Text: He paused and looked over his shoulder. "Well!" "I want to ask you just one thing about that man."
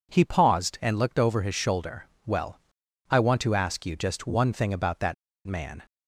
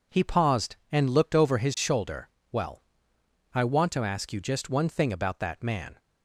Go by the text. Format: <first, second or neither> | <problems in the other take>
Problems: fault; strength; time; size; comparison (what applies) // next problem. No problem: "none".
second | pauses between "that" and "man"; slight; at 5.1 s; 0.31 s long